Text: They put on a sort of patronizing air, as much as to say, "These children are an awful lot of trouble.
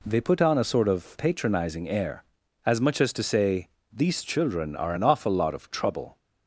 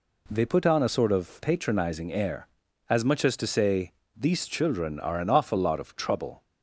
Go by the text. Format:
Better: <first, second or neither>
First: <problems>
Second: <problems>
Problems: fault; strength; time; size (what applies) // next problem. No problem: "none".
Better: neither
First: none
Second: none